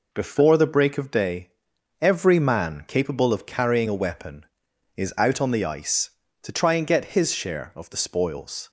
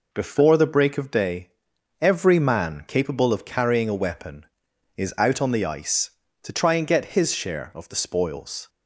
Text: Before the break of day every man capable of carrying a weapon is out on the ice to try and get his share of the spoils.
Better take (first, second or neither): neither